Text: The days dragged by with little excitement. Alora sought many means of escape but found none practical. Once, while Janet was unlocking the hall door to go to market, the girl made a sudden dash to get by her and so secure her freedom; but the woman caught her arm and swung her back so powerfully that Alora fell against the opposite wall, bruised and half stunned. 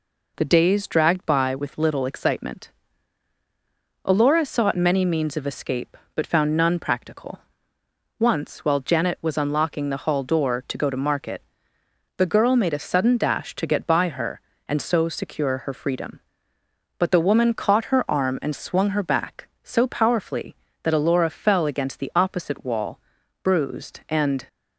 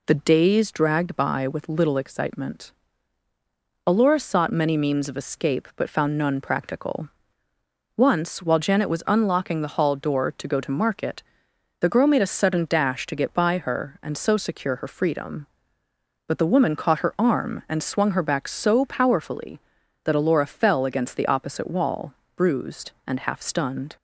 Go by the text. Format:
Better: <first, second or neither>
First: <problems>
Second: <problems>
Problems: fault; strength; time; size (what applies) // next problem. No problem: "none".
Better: second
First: stops before "half stunned"; at 24.4 s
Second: none